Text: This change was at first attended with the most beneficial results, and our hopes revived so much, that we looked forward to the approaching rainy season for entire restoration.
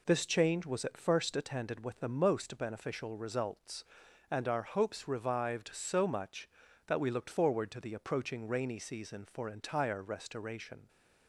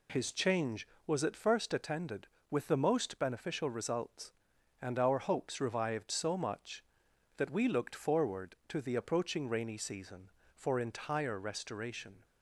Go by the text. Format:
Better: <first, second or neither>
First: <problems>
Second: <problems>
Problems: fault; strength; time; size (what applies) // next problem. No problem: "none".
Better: first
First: none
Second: says "His" for "This"; at 0.1 s